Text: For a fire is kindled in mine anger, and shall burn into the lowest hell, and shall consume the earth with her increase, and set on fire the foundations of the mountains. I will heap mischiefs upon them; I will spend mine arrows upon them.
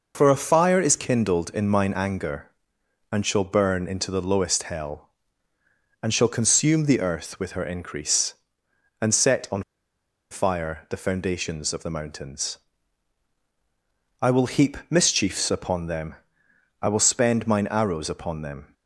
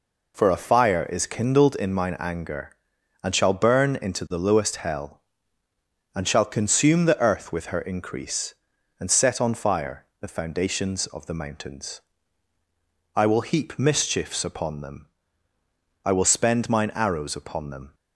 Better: second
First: pauses between "on" and "fire"; noticeable; at 9.6 s; 0.68 s long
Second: none

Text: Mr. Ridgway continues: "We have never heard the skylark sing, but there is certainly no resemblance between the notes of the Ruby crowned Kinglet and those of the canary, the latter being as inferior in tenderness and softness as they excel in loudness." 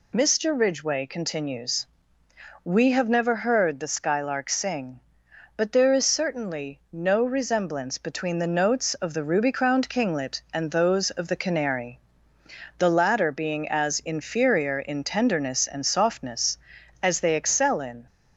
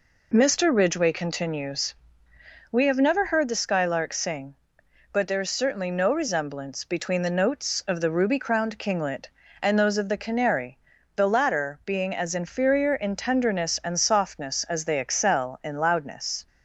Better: second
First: stops before "loudness"; at 18.0 s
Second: none

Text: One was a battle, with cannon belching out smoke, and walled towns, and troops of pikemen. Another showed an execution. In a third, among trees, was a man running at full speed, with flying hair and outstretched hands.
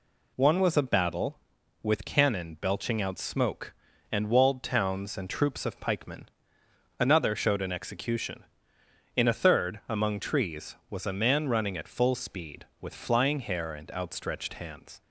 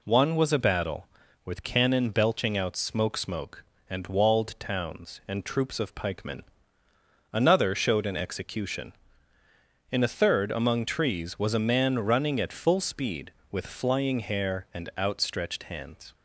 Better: first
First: none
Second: says "smoke" twice; at 3.1 s

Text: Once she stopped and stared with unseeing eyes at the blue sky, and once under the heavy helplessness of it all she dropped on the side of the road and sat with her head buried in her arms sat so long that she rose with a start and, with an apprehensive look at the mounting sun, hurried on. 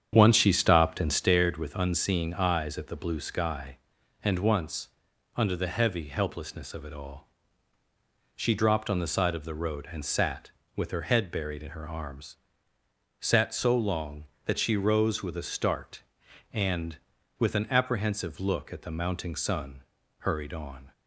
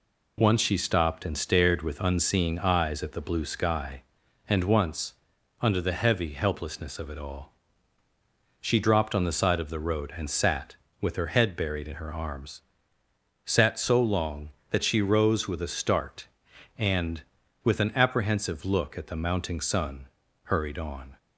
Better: second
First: starts louder than the rest; strong; until 1.4 s; 8.5 dB // pauses between "once" and "under"; noticeable; at 4.8 s; 0.46 s long // pauses between "all" and "she"; at 7.2 s; 1.0 s long // pauses between "arms" and "sat"; noticeable; at 12.3 s; 0.84 s long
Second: pauses between "once" and "under"; noticeable; at 5.1 s; 0.46 s long // pauses between "all" and "she"; at 7.5 s; 1.0 s long // pauses between "arms" and "sat"; noticeable; at 12.6 s; 0.84 s long

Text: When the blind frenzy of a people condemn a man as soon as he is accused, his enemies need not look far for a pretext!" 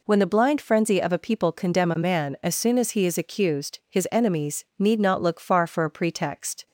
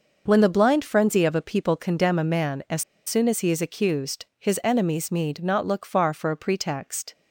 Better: first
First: none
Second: pauses between "as" and "soon"; slight; at 2.8 s; 0.24 s long

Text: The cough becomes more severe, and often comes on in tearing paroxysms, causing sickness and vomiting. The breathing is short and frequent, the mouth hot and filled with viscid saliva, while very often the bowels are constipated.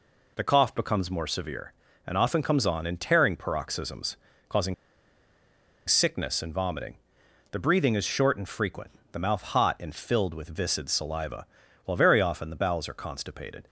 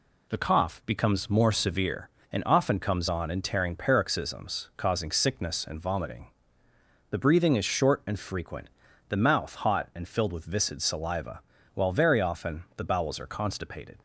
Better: second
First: pauses between "causing" and "sickness"; at 4.7 s; 1.1 s long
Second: none

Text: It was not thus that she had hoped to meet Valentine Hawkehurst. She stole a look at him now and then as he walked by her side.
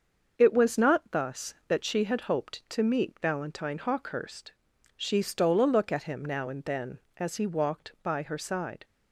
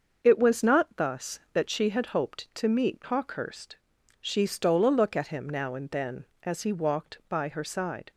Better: first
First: starts louder than the rest; until 1.3 s; 6.5 dB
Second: starts louder than the rest; until 1.2 s; 6.5 dB // skips "Valentine"; at 3.0 s

